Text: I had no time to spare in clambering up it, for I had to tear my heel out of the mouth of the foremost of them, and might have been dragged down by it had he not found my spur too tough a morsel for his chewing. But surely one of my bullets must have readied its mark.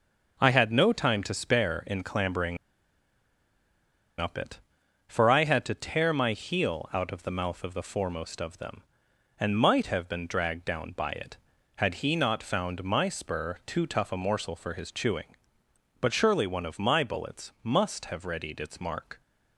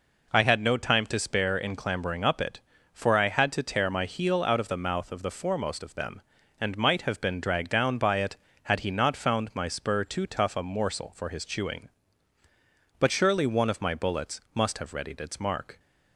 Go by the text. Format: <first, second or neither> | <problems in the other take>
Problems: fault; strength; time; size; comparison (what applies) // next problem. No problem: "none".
second | starts louder than the rest; until 1.4 s; 6.5 dB // pauses between "clambering" and "up"; strong; at 2.5 s; 1.6 s long